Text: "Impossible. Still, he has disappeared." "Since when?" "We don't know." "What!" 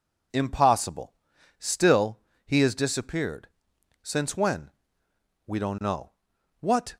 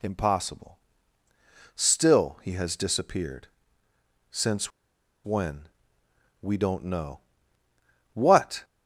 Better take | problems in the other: first | pauses between "Since" and "when"; noticeable; at 4.7 s; 0.54 s long

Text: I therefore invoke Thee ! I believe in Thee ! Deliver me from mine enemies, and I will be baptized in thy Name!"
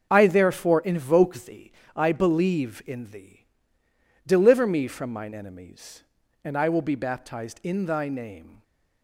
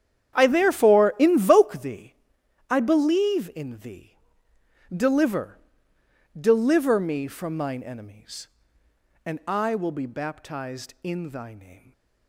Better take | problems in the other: first | starts louder than the rest; strong; until 1.3 s; 9.5 dB; also in the first // says "Deliver" twice; at 6.3 s // stays silent after the last word; slight; from 11.7 s on; 0.5 s long; slight in the first

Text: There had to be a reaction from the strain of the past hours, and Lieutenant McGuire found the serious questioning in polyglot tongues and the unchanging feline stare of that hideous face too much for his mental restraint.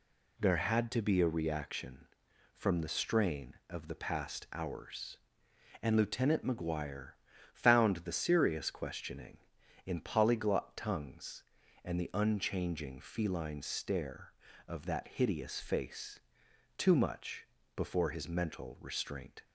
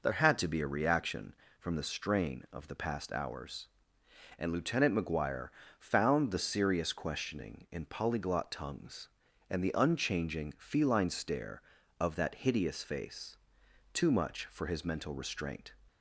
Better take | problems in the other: second | pauses between "McGuire" and "found"; at 7.1 s; 0.42 s long; slight in the second // pauses between "face" and "too"; noticeable; at 16.2 s; 0.56 s long; noticeable in the second // says "before" for "for"; at 17.7 s

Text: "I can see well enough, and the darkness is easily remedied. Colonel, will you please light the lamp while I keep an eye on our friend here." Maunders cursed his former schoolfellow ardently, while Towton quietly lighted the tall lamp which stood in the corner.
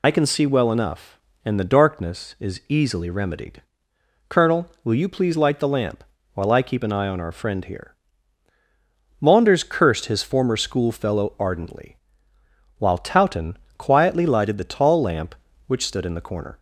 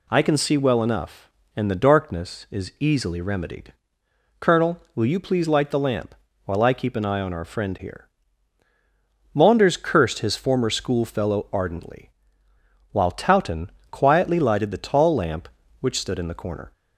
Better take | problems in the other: second | loses the start of "I"; at 0.0 s; 55 ms // pauses between "lamp" and "while"; slight; at 6.0 s; 0.32 s long; slight in the second // pauses between "Towton" and "quietly"; slight; at 13.5 s; 0.20 s long; slight in the second

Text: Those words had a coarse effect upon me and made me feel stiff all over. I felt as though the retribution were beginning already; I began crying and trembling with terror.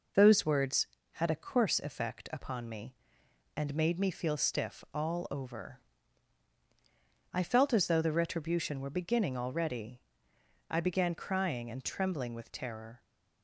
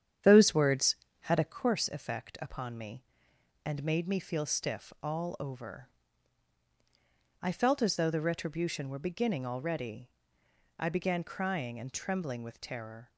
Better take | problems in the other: first | starts louder than the rest; strong; until 1.6 s; 9 dB

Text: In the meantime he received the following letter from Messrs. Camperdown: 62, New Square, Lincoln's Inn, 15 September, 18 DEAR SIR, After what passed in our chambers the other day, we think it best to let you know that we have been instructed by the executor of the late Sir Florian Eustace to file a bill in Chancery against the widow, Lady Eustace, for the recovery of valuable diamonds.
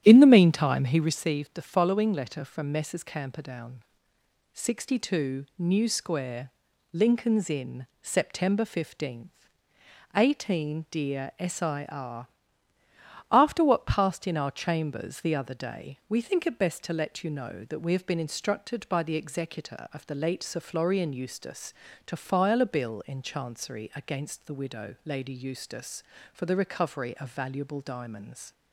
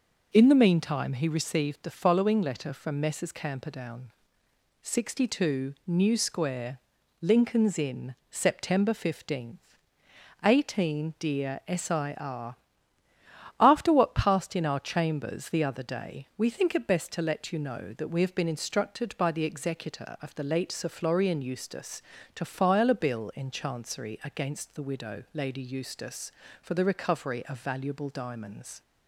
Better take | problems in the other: second | starts louder than the rest; strong; until 1.2 s; 11 dB

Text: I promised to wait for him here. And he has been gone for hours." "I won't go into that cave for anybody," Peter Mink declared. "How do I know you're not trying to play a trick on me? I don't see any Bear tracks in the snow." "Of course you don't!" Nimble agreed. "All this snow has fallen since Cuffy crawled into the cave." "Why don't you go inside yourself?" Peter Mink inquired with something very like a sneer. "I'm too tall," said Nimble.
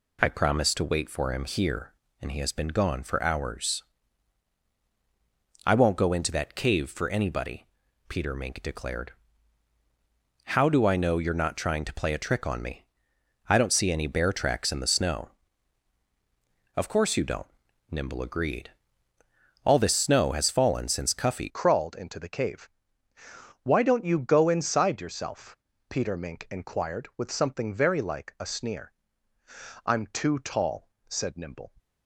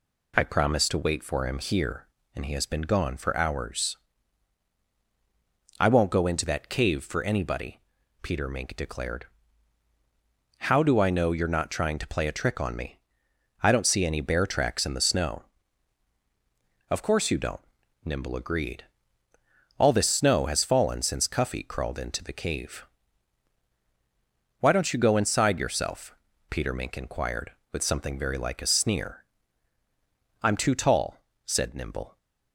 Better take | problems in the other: second | changes voice at "crawled"; from 21.4 s on; 10.3 s long

